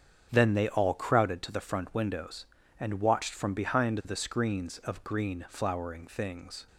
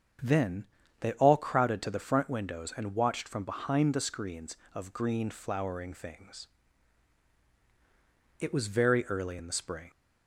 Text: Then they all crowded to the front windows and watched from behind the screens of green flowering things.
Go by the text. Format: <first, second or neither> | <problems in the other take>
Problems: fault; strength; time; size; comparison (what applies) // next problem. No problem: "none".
first | starts louder than the rest; strong; until 1.5 s; 7 dB; strong in the first // pauses between "Then" and "they"; slight; at 0.6 s; 0.34 s long // goes on to say "It was very early in the spring"; from 8.4 s on; 1.4 s long